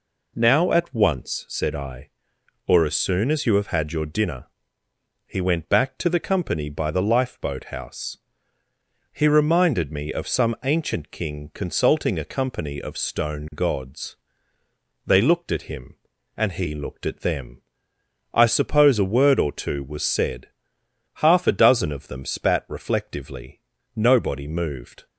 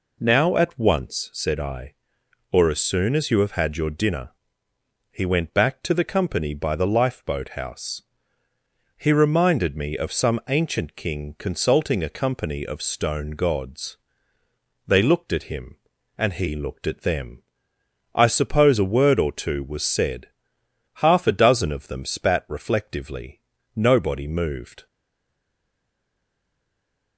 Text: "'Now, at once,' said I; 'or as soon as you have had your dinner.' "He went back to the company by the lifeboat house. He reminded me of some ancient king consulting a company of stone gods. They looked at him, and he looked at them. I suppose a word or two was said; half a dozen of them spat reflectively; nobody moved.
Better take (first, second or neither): first